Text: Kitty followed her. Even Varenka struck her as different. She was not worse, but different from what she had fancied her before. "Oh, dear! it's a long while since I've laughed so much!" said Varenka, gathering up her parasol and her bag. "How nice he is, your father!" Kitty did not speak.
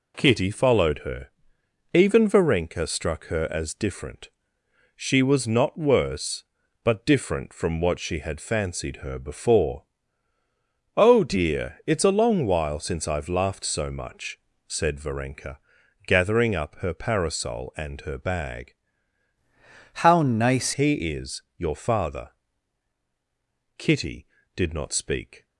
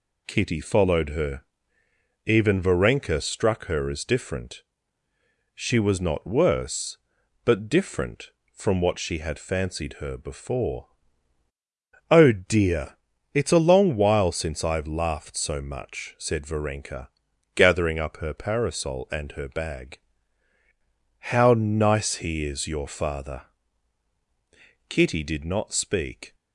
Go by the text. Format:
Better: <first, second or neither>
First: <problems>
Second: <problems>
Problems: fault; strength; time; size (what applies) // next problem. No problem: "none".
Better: second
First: changes voice from "How" to "nice"; from 19.9 to 20.7 s; 0.8 s long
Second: none